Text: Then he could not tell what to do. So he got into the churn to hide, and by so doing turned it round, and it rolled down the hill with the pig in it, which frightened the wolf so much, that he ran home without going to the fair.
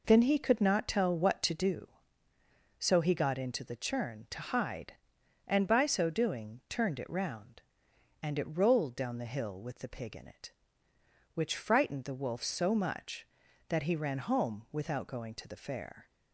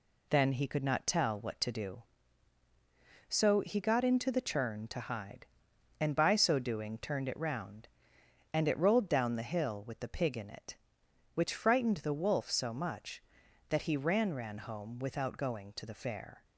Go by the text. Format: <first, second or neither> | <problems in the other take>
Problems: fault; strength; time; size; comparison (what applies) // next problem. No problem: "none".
first | says "ran" twice; at 14.3 s